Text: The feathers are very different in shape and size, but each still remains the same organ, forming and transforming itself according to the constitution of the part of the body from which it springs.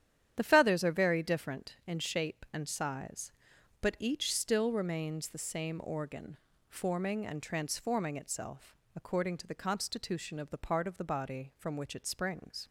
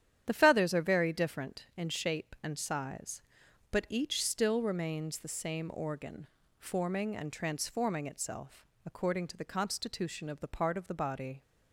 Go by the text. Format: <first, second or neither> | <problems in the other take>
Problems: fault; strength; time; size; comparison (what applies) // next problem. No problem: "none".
first | starts louder than the rest; strong; until 1.2 s; 10 dB; strong in the first // pauses between "itself" and "according"; slight; at 8.6 s; 0.20 s long; slight in the first // stops before "from which it springs"; at 11.4 s